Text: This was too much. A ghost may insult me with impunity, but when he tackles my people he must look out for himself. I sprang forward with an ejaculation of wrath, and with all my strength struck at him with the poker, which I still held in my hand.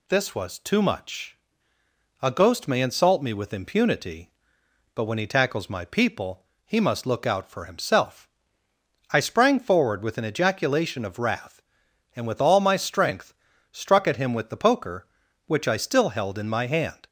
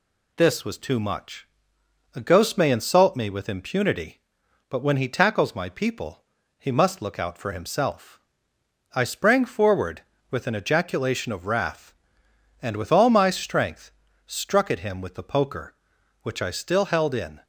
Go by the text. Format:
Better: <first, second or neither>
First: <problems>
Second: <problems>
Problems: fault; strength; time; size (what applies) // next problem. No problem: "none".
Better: first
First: pauses between "people" and "he"; slight; at 6.4 s; 0.20 s long // pauses between "strength" and "struck"; at 13.3 s; 0.38 s long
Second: pauses between "people" and "he"; slight; at 6.2 s; 0.36 s long // pauses between "strength" and "struck"; slight; at 13.9 s; 0.34 s long // stops before "my hand"; at 17.4 s